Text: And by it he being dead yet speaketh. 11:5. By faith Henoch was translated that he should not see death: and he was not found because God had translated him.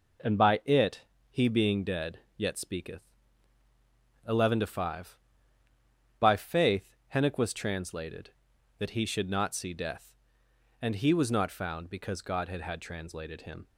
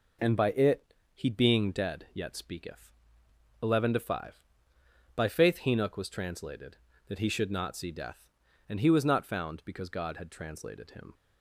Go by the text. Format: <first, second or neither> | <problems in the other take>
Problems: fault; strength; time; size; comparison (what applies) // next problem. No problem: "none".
second | pauses between "it" and "he"; slight; at 1.0 s; 0.28 s long; slight in the second // pauses between "dead" and "yet"; slight; at 2.1 s; 0.18 s long // pauses between "faith" and "Henoch"; slight; at 6.9 s; 0.20 s long // says "had" twice; at 12.6 s